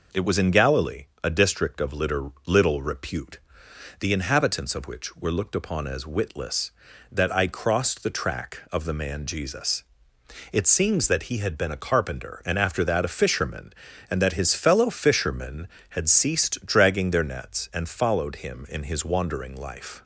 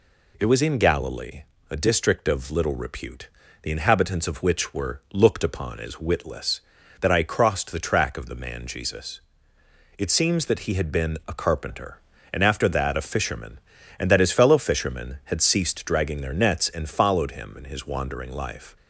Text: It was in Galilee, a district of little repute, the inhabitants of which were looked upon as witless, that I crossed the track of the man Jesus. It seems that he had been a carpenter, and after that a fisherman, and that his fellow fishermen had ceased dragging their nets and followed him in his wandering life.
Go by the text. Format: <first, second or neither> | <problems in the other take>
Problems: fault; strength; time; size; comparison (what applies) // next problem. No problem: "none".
second | says "little" twice; at 2.4 s